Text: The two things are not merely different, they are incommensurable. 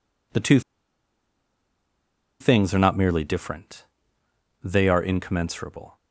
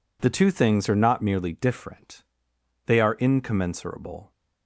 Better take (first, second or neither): second